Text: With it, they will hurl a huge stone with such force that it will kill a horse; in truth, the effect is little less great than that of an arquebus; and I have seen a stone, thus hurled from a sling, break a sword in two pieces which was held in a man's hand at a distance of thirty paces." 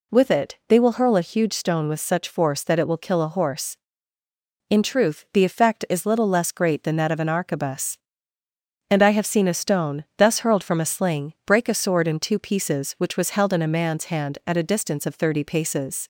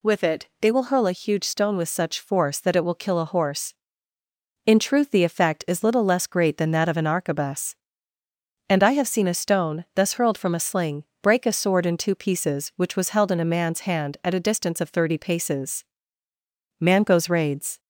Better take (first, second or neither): first